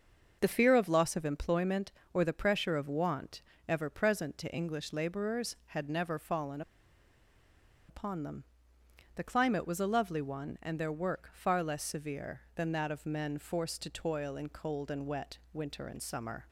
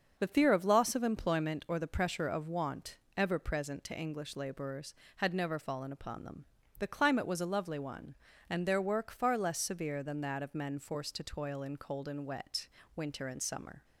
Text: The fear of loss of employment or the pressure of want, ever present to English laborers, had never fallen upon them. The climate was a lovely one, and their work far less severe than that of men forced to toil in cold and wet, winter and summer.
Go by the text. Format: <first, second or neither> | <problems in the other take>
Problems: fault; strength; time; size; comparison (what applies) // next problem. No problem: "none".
second | starts louder than the rest; noticeable; until 1.4 s; 6 dB; also in the second // pauses between "fallen" and "upon"; strong; at 6.6 s; 1.2 s long